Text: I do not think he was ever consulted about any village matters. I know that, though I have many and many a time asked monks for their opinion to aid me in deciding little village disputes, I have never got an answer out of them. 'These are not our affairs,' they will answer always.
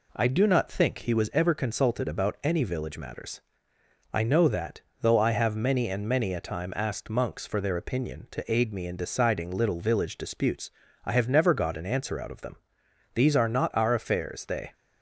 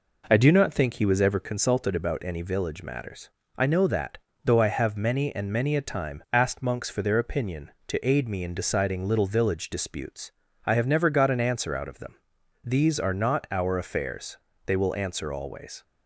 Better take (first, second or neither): second